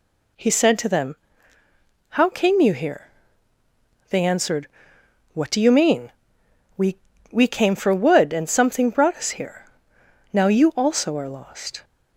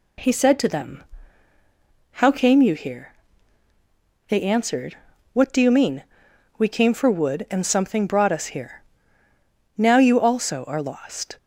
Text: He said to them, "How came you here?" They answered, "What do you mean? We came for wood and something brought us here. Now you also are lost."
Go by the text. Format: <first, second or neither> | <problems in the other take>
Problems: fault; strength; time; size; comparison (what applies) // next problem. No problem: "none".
second | says "We" twice; at 7.3 s